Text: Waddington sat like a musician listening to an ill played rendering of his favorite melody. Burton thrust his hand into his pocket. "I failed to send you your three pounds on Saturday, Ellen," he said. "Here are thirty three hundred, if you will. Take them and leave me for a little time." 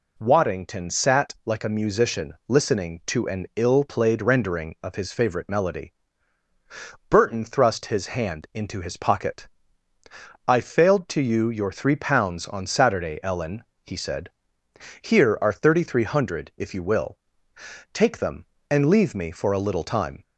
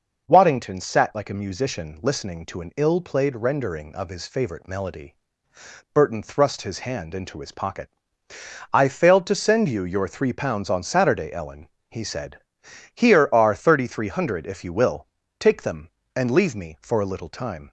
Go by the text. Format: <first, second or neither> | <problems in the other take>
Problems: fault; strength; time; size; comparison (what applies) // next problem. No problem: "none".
second | pauses between "musician" and "listening"; slight; at 2.3 s; 0.16 s long // skips "send"; at 11.2 s